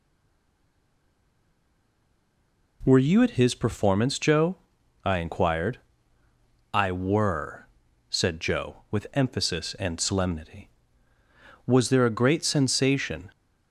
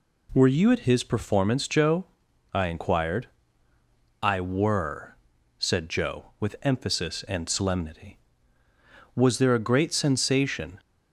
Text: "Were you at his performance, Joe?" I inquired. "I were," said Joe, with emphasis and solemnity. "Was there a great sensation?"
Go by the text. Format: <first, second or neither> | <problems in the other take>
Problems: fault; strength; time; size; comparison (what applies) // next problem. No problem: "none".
second | stays silent before the first word; strong; until 2.8 s; 2.8 s long